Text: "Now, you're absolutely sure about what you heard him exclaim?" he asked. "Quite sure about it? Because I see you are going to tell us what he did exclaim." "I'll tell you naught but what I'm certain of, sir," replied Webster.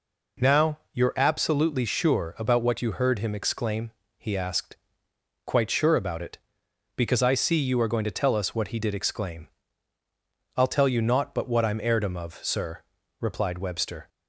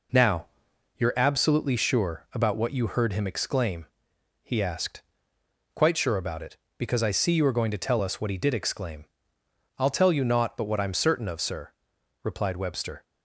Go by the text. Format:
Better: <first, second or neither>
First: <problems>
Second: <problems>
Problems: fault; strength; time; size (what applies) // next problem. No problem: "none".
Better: second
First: says "heirdom" for "certain"; at 11.8 s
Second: none